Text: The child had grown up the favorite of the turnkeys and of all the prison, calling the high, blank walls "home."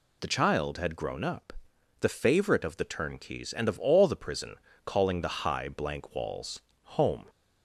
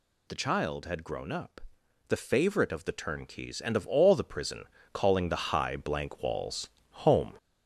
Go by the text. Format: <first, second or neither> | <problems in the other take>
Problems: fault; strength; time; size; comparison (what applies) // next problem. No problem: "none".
first | gets louder; noticeable; throughout; 4.5 dB // pauses between "up" and "the"; noticeable; at 1.6 s; 0.48 s long; noticeable in the first // pauses between "walls" and "home"; slight; at 6.6 s; 0.24 s long; slight in the first